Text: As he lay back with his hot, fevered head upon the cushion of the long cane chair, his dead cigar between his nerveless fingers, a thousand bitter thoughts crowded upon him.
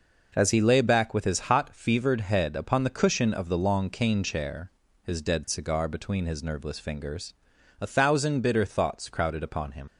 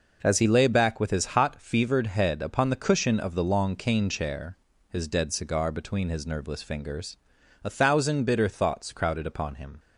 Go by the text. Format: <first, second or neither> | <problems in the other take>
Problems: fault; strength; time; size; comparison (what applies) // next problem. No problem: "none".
second | leaves "him" unfinished; at 9.8 s; 85 ms